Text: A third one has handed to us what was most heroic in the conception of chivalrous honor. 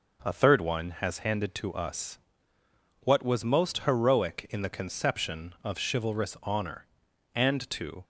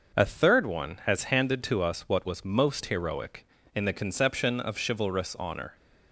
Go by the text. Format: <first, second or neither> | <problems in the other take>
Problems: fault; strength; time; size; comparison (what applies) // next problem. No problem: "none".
second | pauses between "us" and "what"; noticeable; at 2.1 s; 0.86 s long // goes on to say "And to"; noticeable; from 7.3 s on; 0.70 s long